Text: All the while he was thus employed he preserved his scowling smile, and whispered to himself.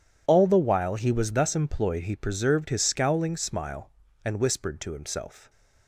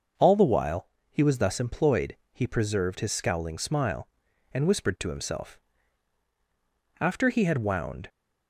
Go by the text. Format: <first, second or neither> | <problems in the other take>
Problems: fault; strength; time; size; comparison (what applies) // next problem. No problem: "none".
first | pauses between "while" and "he"; slight; at 0.8 s; 0.24 s long // pauses between "employed" and "he"; slight; at 2.1 s; 0.18 s long // goes on to say "After he had wound"; noticeable; from 7.0 s on; 1.0 s long